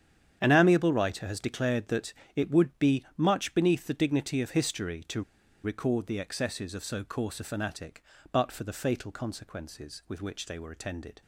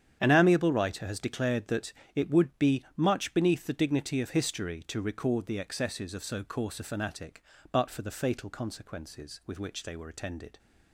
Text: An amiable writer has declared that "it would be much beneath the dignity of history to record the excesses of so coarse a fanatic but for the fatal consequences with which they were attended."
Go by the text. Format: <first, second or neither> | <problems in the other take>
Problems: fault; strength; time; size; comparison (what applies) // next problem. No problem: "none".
second | starts louder than the rest; strong; until 1.4 s; 9 dB; strong in the second // pauses between "that" and "it"; slight; at 2.1 s; 0.24 s long; slight in the second // pauses between "to" and "record"; at 5.2 s; 0.42 s long